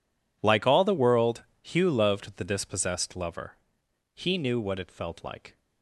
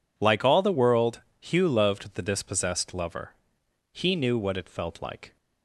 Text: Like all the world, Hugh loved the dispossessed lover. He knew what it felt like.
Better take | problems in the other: second | gets quieter; strong; throughout; 19 dB

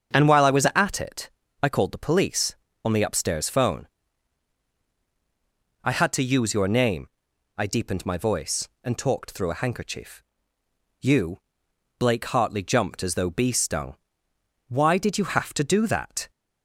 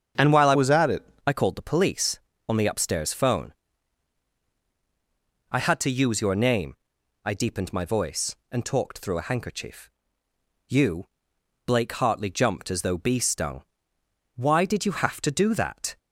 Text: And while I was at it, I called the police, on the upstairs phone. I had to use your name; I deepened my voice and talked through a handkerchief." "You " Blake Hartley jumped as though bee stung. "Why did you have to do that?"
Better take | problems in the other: first | starts louder than the rest; strong; until 1.3 s; 8 dB; strong in the first // changes voice from "was" to "it"; from 0.5 to 1.0 s; 0.5 s long

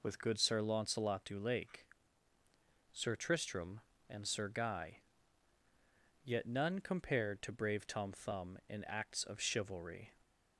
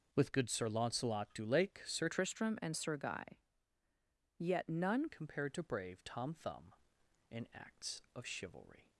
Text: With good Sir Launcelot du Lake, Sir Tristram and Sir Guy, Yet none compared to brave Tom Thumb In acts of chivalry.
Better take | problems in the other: first | changes voice from "Tristram" to "none"; from 2.0 to 5.0 s; 3.0 s long

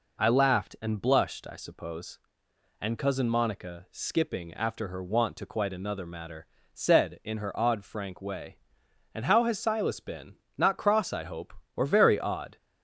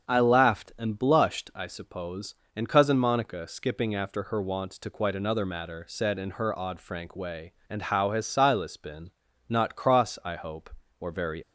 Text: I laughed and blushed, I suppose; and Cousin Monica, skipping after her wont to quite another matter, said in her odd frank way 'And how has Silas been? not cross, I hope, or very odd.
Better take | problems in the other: first | starts louder than the rest; until 1.1 s; 7 dB // stops before "odd"; at 11.4 s

